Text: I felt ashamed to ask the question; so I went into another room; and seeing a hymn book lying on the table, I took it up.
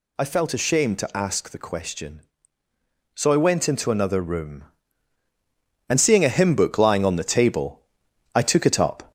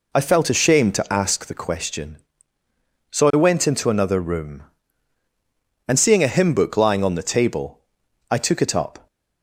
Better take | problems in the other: second | gets louder; slight; throughout; 2.5 dB

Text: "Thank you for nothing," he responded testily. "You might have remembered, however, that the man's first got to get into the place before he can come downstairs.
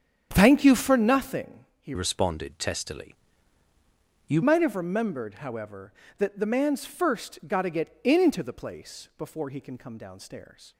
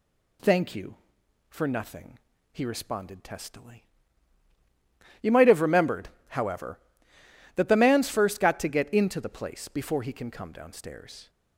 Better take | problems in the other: second | starts louder than the rest; strong; until 1.3 s; 8.5 dB // changes voice from "responded" to "You"; from 1.9 to 4.4 s; 2.5 s long

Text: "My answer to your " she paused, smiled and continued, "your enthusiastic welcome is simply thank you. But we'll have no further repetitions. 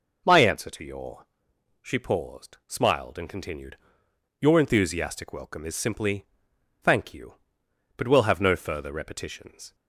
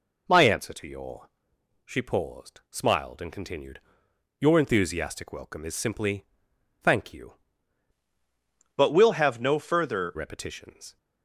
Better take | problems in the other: first | pauses between "simply" and "thank"; noticeable; at 6.2 s; 0.58 s long; noticeable in the first // changes voice from "But" to "further"; from 8.7 to 10.1 s; 1.4 s long

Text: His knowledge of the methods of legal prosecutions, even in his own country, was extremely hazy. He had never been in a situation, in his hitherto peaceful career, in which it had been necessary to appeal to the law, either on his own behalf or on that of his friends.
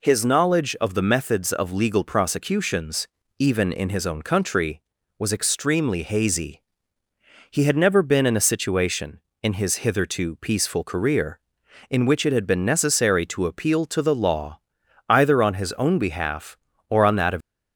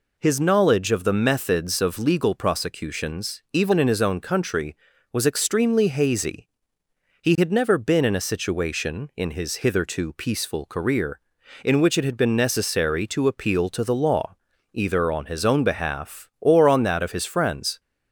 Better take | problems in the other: second | stops before "his friends"; at 17.4 s

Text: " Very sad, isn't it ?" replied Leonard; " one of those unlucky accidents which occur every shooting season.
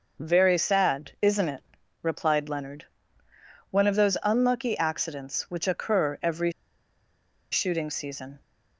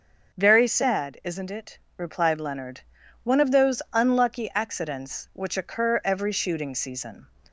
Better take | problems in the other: second | pauses between "every" and "shooting"; at 6.5 s; 1.0 s long

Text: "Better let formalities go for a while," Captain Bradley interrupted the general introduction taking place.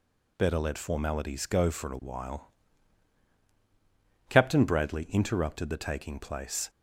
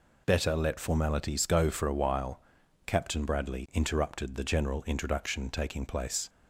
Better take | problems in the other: second | skips "general introduction"; at 5.7 s

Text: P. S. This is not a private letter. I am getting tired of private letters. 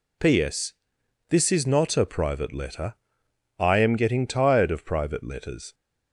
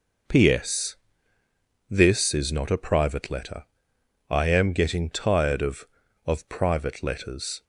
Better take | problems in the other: first | says "of" twice; at 6.2 s

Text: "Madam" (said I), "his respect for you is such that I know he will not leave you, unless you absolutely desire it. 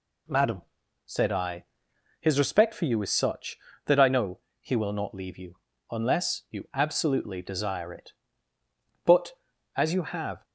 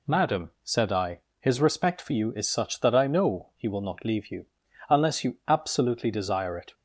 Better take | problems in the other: second | pauses between "know" and "he"; slight; at 4.3 s; 0.20 s long // goes on to say "But as you have"; from 9.0 s on; 1.4 s long

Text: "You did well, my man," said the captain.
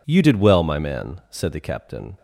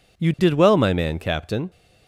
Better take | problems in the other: first | skips "said the"; at 1.1 s

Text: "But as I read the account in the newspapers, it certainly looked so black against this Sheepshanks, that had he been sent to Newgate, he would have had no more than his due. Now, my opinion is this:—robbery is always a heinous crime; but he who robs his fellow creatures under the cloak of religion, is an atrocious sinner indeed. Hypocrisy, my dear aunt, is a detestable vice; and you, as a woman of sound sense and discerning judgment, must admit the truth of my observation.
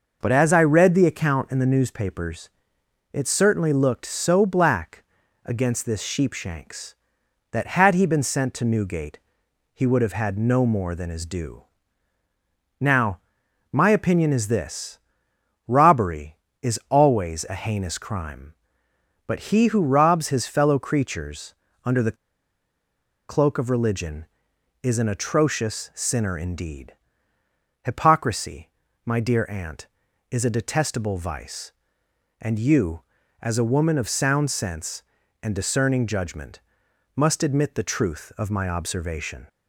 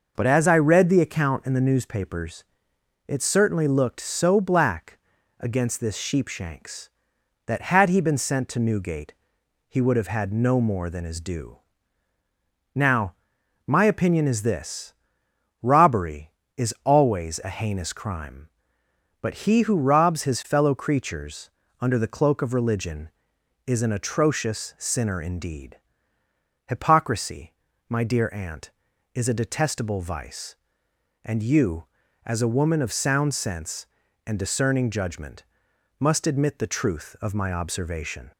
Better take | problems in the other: second | pauses between "black" and "against"; at 5.0 s; 0.40 s long; also in the second // pauses between "creatures" and "under"; slight; at 21.5 s; 0.28 s long; slight in the second // pauses between "the" and "cloak"; at 22.1 s; 1.1 s long

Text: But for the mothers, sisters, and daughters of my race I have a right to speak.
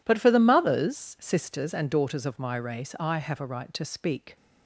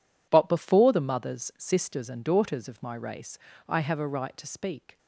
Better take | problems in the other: first | says "before" for "for"; at 0.4 s // pauses between "race" and "I"; slight; at 3.3 s; 0.30 s long

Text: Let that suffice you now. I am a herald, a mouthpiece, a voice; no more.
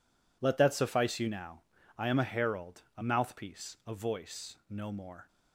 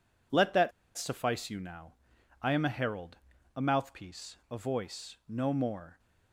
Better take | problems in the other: first | pauses between "that" and "suffice"; slight; at 0.7 s; 0.25 s long

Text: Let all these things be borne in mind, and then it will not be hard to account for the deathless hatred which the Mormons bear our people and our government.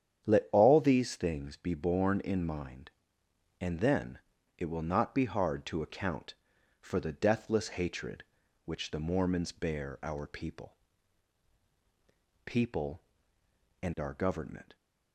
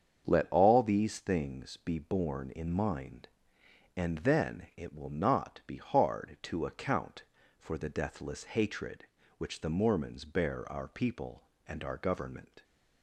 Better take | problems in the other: second | starts louder than the rest; strong; until 1.2 s; 9 dB; strong in the second // pauses between "then" and "it"; slight; at 4.2 s; 0.36 s long // says "people" twice; at 12.4 s

